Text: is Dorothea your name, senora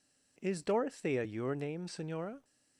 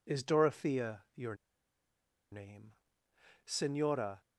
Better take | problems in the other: first | pauses between "your" and "name"; noticeable; at 1.3 s; 0.97 s long

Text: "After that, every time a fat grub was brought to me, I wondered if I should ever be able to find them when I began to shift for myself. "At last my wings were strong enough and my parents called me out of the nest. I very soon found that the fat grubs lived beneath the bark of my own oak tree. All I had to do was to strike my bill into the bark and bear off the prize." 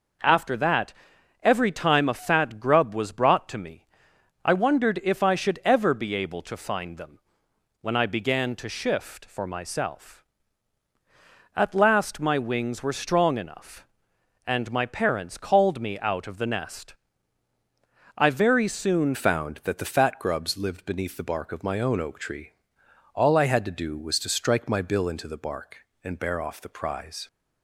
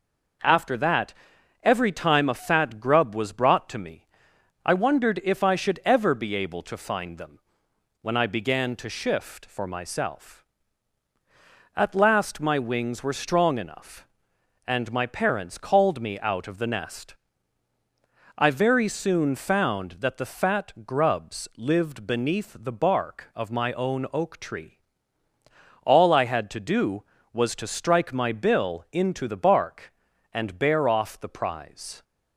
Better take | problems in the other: second | pauses between "them" and "when"; noticeable; at 7.1 s; 0.64 s long; noticeable in the second // changes voice at "found"; from 19.1 s on; 8.1 s long

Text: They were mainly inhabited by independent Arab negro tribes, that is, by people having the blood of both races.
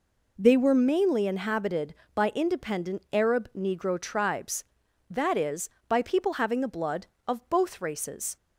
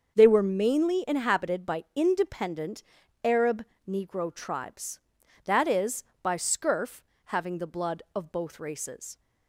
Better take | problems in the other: first | starts louder than the rest; until 1.1 s; 6.5 dB // pauses between "independent" and "Arab"; at 2.8 s; 0.42 s long // pauses between "Arab" and "negro"; slight; at 3.6 s; 0.24 s long // says "scurf" for "people"; at 6.3 s

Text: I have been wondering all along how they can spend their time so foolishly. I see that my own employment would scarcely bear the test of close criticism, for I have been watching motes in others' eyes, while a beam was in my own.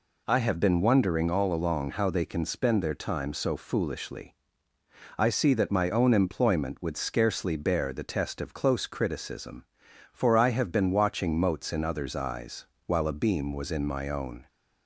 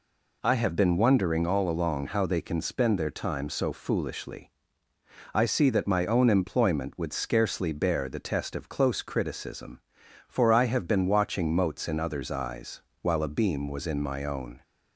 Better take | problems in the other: neither | none

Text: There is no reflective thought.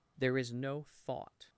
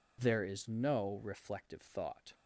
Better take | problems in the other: second | skips "reflective"; at 0.8 s

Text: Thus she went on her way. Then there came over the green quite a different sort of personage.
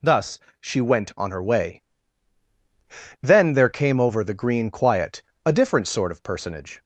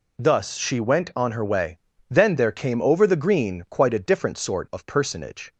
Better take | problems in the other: second | pauses between "Thus" and "she"; slight; at 0.3 s; 0.20 s long // says "quiet" for "quite"; at 4.7 s

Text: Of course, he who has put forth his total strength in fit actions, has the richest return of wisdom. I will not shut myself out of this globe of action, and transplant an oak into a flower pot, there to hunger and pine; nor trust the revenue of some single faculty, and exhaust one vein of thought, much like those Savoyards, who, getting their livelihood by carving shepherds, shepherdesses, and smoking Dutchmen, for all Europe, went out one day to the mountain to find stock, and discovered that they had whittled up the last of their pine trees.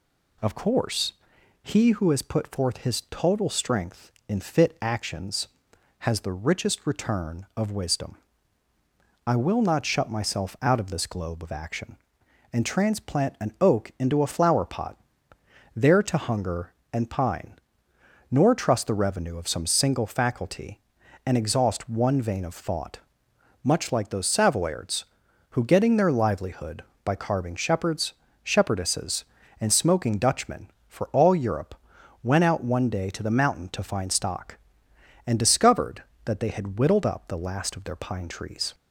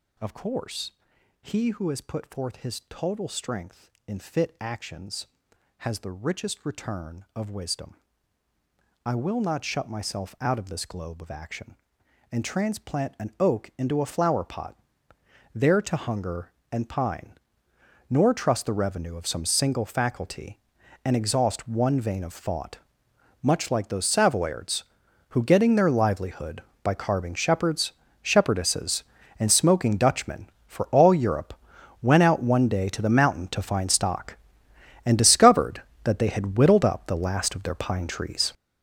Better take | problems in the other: first | gets louder; strong; throughout; 11 dB

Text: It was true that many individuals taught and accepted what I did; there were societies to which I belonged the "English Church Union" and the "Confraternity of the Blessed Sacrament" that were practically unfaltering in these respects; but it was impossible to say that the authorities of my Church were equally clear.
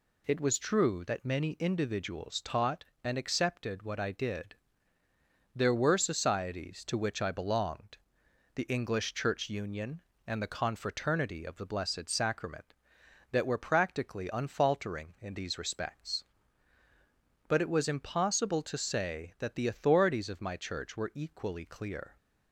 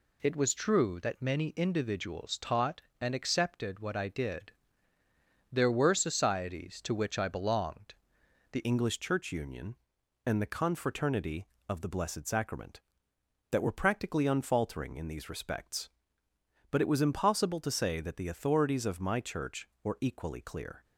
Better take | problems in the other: first | pauses between "belonged" and "the"; noticeable; at 7.9 s; 0.56 s long; noticeable in the first // changes voice at "English"; from 8.6 s on; 12.2 s long

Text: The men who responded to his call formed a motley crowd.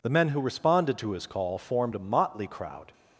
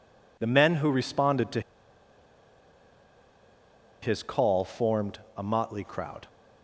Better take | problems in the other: first | pauses between "to" and "his"; strong; at 1.6 s; 2.4 s long // pauses between "formed" and "a"; slight; at 5.1 s; 0.18 s long

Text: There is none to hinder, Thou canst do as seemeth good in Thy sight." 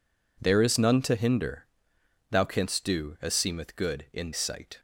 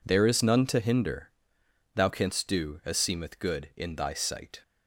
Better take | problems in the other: second | skips "Thy"; at 4.3 s

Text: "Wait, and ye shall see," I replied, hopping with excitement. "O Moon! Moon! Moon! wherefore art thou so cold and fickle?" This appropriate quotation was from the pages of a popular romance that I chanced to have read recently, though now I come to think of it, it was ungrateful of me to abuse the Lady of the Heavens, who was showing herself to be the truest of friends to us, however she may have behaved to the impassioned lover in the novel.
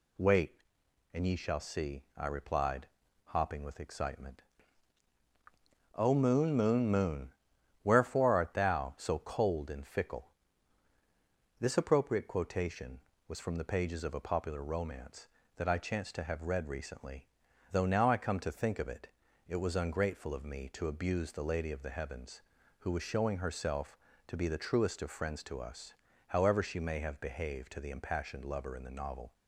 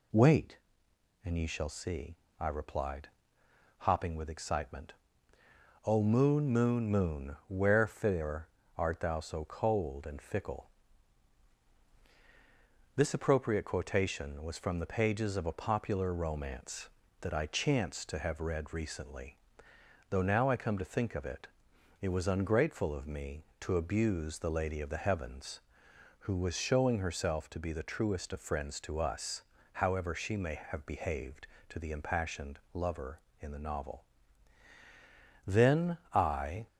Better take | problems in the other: first | pauses between "wherefore" and "art"; slight; at 8.4 s; 0.30 s long // goes on to say "Then I"; noticeable; from 35.4 s on; 1.2 s long

